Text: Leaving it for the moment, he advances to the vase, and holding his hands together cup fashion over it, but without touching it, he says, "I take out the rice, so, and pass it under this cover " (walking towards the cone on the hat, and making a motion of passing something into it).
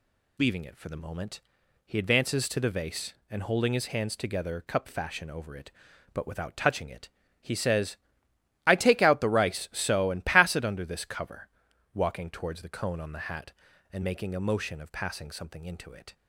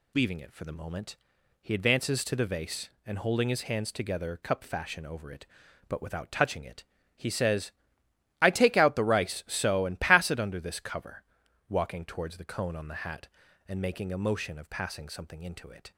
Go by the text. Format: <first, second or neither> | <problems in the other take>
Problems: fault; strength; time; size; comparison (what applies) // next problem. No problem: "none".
neither | none